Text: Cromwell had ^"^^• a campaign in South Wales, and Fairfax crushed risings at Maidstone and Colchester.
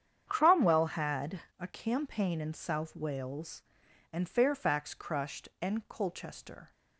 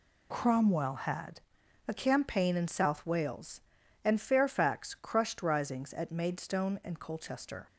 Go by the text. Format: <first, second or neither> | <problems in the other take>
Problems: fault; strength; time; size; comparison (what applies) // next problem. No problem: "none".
second | starts louder than the rest; strong; until 1.2 s; 8.5 dB // skips "risings at Maidstone"; at 5.5 s